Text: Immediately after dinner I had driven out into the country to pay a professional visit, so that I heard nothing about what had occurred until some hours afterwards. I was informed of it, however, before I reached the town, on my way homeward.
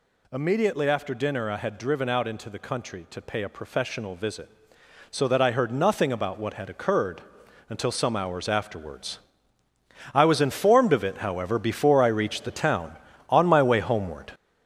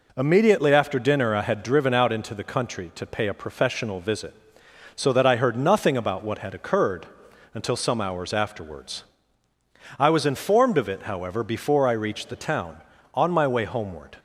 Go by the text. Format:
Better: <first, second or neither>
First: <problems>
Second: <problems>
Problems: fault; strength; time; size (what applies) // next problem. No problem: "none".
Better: second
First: gets louder; throughout; 7 dB // pauses between "occurred" and "until"; noticeable; at 7.2 s; 0.48 s long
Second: pauses between "occurred" and "until"; noticeable; at 7.0 s; 0.48 s long